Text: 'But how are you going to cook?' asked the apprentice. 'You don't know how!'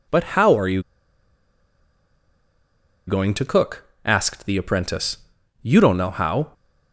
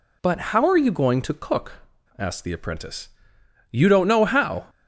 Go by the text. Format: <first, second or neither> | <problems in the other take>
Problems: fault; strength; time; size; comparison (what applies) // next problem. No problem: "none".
second | pauses between "you" and "going"; strong; at 0.8 s; 2.2 s long